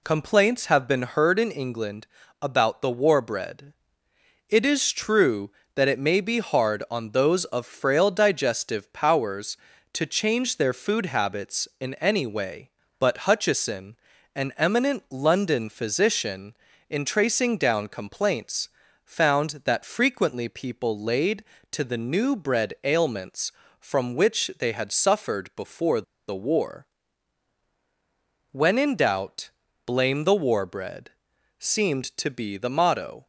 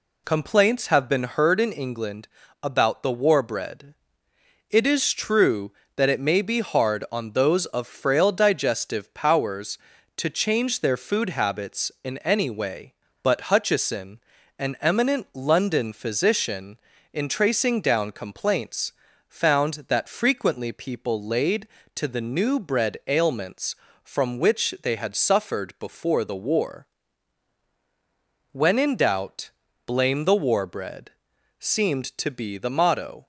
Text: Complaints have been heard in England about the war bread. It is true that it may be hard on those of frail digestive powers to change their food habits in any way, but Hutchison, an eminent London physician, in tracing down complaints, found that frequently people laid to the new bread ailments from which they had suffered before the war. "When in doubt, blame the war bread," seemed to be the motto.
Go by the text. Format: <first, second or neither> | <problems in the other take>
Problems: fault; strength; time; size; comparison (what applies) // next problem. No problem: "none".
second | pauses between "England" and "about"; slight; at 2.0 s; 0.36 s long; slight in the second // pauses between "before" and "the"; slight; at 26.0 s; 0.27 s long